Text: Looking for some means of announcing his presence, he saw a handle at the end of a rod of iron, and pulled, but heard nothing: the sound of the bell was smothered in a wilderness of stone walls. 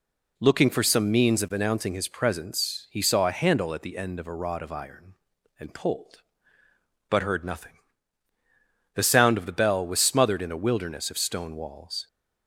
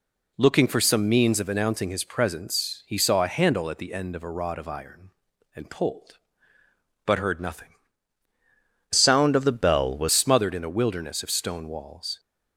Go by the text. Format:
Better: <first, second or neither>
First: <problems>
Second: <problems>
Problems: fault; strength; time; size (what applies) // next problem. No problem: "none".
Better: first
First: none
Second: changes voice from "sound" to "was"; from 8.9 to 10.0 s; 1.1 s long